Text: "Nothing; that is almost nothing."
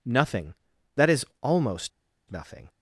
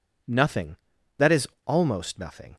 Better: second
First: pauses between "is" and "almost"; slight; at 1.2 s; 0.16 s long // pauses between "almost" and "nothing"; at 1.9 s; 0.40 s long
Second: pauses between "is" and "almost"; slight; at 1.4 s; 0.18 s long

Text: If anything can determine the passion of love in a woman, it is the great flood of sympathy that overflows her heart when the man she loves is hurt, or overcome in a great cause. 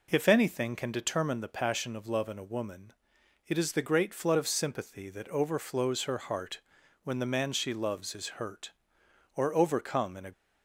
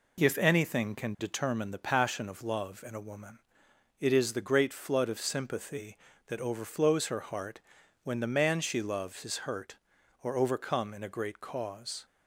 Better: second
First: pauses between "heart" and "when"; at 6.6 s; 0.42 s long // stops before "great cause"; at 10.3 s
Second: pauses between "heart" and "when"; noticeable; at 7.5 s; 0.46 s long

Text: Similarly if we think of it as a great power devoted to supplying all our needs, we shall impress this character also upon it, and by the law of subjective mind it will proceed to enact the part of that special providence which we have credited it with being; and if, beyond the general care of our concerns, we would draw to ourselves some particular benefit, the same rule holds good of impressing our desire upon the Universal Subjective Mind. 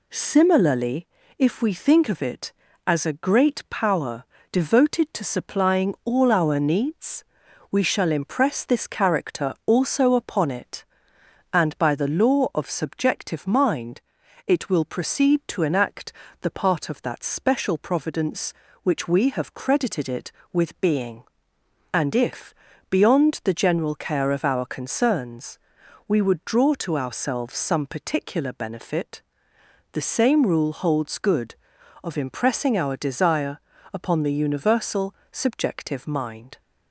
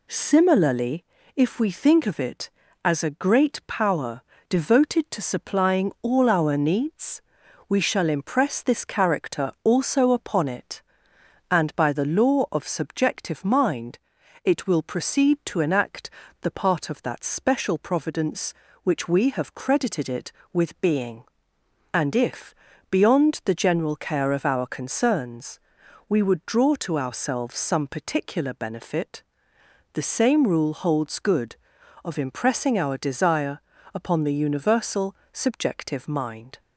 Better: neither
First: pauses between "Similarly" and "if"; slight; at 1.0 s; 0.30 s long // pauses between "power" and "devoted"; slight; at 4.2 s; 0.26 s long // pauses between "mind" and "it"; at 14.0 s; 0.44 s long // pauses between "enact" and "the"; slight; at 16.1 s; 0.30 s long // pauses between "desire" and "upon"; slight; at 33.5 s; 0.34 s long // pauses between "Universal" and "Subjective"; slight; at 35.1 s; 0.20 s long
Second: pauses between "Similarly" and "if"; slight; at 1.0 s; 0.30 s long // pauses between "power" and "devoted"; slight; at 4.2 s; 0.26 s long // pauses between "mind" and "it"; at 13.9 s; 0.44 s long // pauses between "enact" and "the"; slight; at 16.0 s; 0.32 s long // pauses between "desire" and "upon"; slight; at 33.5 s; 0.34 s long // pauses between "Universal" and "Subjective"; slight; at 35.1 s; 0.20 s long

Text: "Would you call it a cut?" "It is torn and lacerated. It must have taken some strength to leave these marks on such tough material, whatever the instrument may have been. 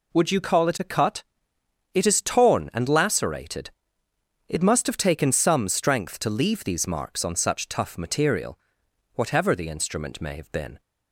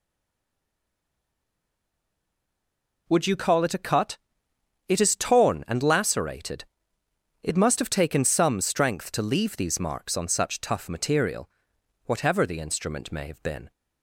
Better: first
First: none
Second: stays silent before the first word; strong; until 3.0 s; 3.0 s long

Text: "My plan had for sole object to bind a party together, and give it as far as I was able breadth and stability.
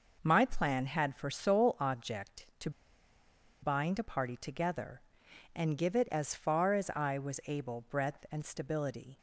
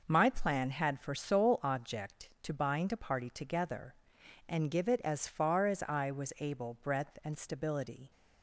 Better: second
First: pauses between "to" and "bind"; noticeable; at 2.6 s; 0.92 s long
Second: none

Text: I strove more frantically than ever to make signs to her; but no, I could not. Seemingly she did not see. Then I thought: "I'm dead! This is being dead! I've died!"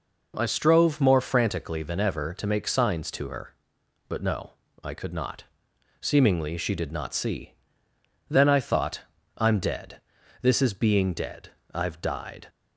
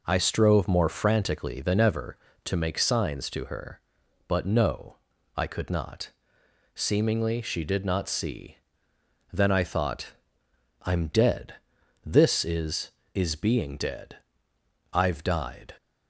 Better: first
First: none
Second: says "is" twice; at 13.1 s

